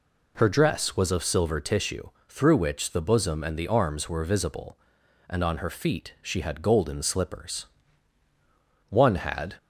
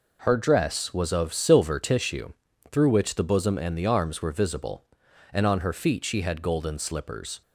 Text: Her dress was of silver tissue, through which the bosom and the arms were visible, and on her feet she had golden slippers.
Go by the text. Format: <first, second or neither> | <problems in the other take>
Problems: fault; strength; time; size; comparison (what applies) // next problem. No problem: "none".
second | goes on to say "One had"; noticeable; from 8.9 s on; 0.66 s long